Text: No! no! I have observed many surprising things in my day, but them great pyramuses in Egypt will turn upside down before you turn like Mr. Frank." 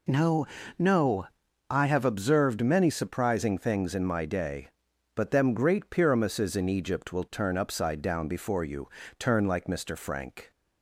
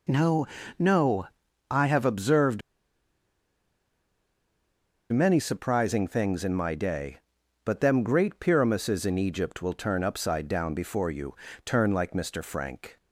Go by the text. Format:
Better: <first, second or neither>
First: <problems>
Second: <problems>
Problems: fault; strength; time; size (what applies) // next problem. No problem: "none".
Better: first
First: pauses between "you" and "turn"; slight; at 8.8 s; 0.32 s long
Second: pauses between "observed" and "many"; strong; at 2.6 s; 2.5 s long // pauses between "you" and "turn"; slight; at 11.3 s; 0.32 s long